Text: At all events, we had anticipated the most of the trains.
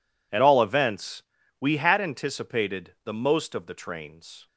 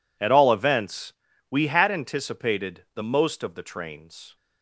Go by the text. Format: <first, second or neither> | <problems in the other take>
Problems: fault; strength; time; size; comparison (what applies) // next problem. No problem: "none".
neither | none